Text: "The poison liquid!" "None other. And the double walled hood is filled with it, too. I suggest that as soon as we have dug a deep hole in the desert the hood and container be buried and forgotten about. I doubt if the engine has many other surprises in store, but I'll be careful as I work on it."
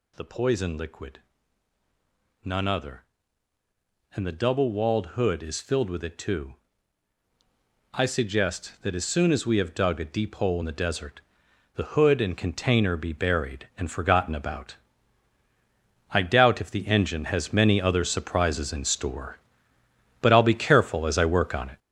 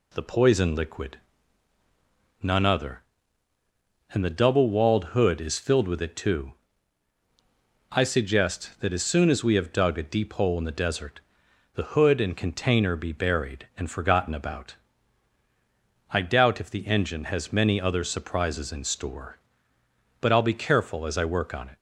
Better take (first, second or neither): second